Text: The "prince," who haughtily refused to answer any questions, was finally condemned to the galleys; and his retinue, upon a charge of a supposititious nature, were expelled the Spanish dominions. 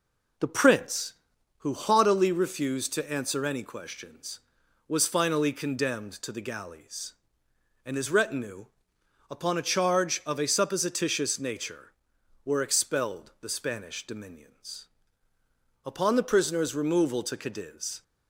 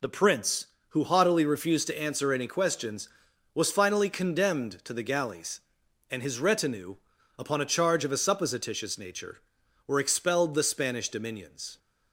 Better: second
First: goes on to say "Upon the prisoner's removal to Cadiz"; strong; from 15.8 s on; 2.1 s long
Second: none

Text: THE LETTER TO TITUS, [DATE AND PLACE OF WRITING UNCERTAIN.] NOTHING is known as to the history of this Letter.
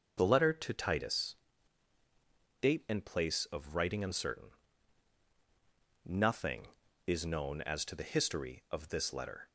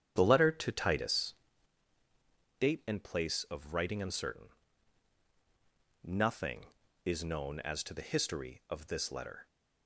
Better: first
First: none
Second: starts louder than the rest; strong; until 1.7 s; 9 dB

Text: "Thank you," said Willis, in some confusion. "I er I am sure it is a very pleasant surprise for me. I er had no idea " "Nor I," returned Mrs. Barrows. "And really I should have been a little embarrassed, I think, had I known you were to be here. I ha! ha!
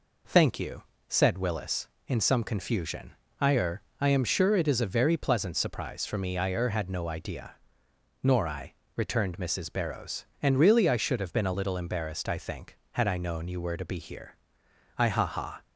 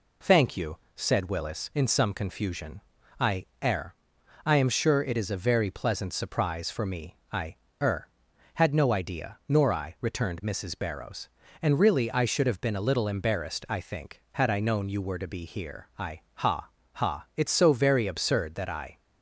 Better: first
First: pauses between "er" and "I"; slight; at 3.8 s; 0.18 s long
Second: pauses between "I" and "er"; slight; at 3.4 s; 0.18 s long // pauses between "er" and "I"; noticeable; at 3.9 s; 0.50 s long // pauses between "I" and "er"; slight; at 7.5 s; 0.26 s long // goes on to say "it's so very absurd that I"; from 17.3 s on; 1.6 s long

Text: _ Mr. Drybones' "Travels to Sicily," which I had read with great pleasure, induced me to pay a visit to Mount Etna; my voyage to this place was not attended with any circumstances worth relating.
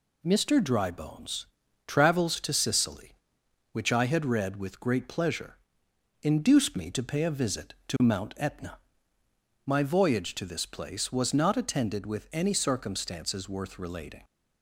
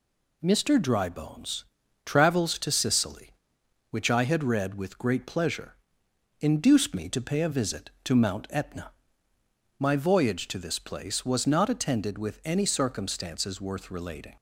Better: neither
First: pauses between "Drybones" and "Travels"; at 1.4 s; 0.40 s long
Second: pauses between "Drybones" and "Travels"; at 1.6 s; 0.40 s long

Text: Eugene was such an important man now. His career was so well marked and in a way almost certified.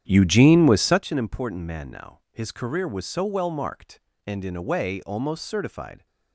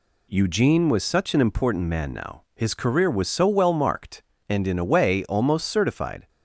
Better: second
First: starts louder than the rest; strong; until 1.0 s; 9.5 dB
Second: none

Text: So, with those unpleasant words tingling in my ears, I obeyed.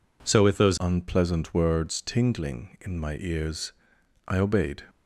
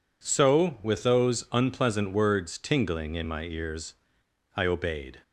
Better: second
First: changes voice at "unpleasant"; from 0.8 s on; 4.0 s long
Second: none

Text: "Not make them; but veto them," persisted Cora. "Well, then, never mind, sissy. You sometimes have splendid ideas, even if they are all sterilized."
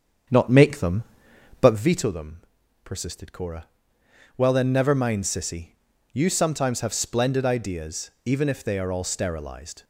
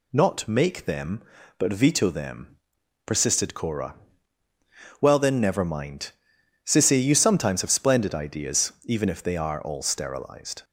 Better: second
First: starts louder than the rest; strong; until 1.8 s; 8 dB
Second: none

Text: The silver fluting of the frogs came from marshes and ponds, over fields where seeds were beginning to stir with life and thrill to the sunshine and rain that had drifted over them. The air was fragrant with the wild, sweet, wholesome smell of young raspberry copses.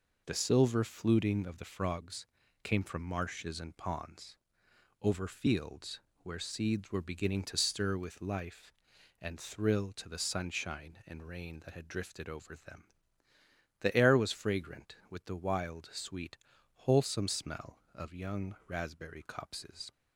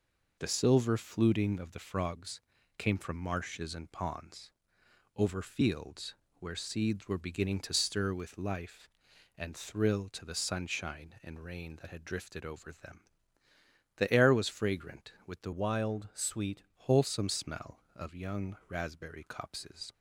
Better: first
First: pauses between "frogs" and "came"; slight; at 2.2 s; 0.36 s long // pauses between "fields" and "where"; slight; at 5.9 s; 0.22 s long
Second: pauses between "frogs" and "came"; slight; at 2.4 s; 0.36 s long // pauses between "fields" and "where"; slight; at 6.1 s; 0.24 s long // changes voice from "wild" to "sweet"; from 15.5 to 16.6 s; 1.1 s long

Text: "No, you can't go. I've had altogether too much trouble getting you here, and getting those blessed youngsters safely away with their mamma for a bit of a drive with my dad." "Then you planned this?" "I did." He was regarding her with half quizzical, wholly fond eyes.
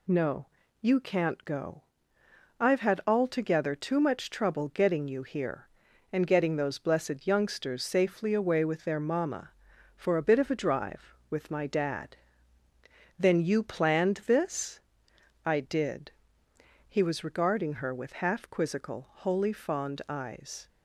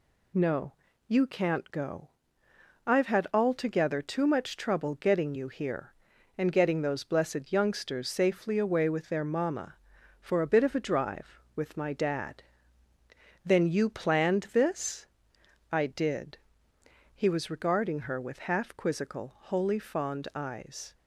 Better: neither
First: none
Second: none

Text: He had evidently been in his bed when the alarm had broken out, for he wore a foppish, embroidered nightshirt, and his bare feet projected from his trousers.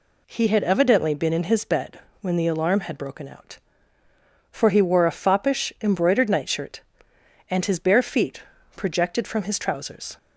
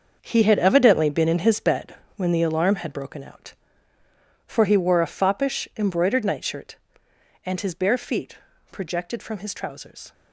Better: first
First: pauses between "bed" and "when"; slight; at 1.9 s; 0.22 s long // pauses between "feet" and "projected"; slight; at 8.4 s; 0.34 s long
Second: gets quieter; strong; throughout; 11 dB // pauses between "bed" and "when"; slight; at 1.9 s; 0.22 s long // pauses between "feet" and "projected"; slight; at 8.3 s; 0.34 s long

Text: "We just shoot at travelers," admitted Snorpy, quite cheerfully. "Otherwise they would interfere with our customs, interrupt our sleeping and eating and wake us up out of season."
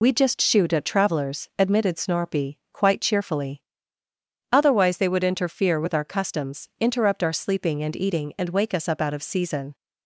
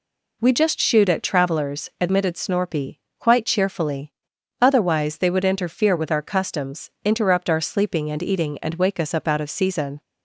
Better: second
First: loses the start of "We"; at 0.0 s; 40 ms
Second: none

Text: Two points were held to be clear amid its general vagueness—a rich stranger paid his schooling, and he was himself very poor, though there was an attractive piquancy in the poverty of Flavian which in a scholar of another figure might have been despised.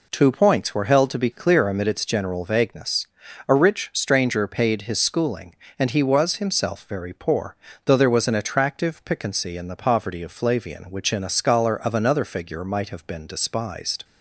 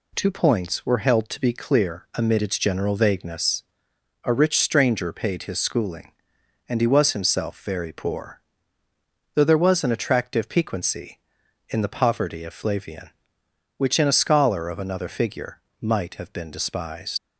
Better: first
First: none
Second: pauses between "figure" and "might"; slight; at 15.5 s; 0.20 s long // leaves "despised" unfinished; at 17.1 s; 115 ms

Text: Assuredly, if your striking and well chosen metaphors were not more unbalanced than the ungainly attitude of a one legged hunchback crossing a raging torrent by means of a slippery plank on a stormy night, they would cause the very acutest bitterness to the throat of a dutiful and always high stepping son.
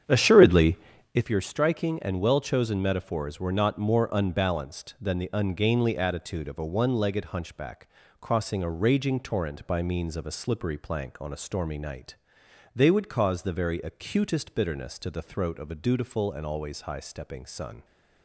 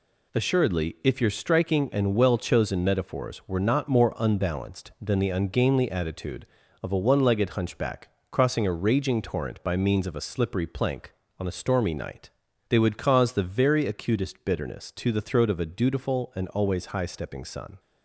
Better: second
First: starts louder than the rest; strong; until 1.3 s; 8.5 dB // pauses between "hunchback" and "crossing"; slight; at 7.8 s; 0.32 s long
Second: pauses between "hunchback" and "crossing"; slight; at 8.0 s; 0.20 s long

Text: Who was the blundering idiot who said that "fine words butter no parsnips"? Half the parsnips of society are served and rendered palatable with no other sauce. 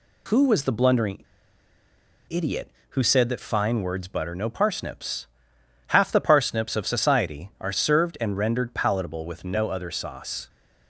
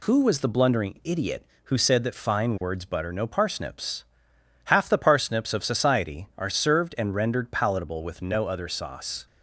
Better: second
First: pauses between "blundering" and "idiot"; at 1.2 s; 1.0 s long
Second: none

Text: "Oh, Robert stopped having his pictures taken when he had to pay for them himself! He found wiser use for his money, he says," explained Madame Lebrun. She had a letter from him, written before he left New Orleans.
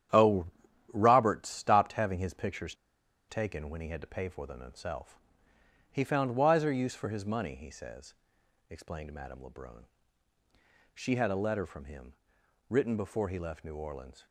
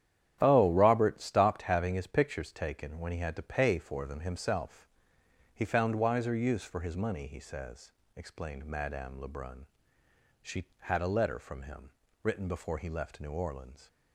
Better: second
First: starts louder than the rest; strong; until 1.5 s; 10 dB // pauses between "pictures" and "taken"; noticeable; at 2.7 s; 0.55 s long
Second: starts louder than the rest; strong; until 1.4 s; 10.5 dB

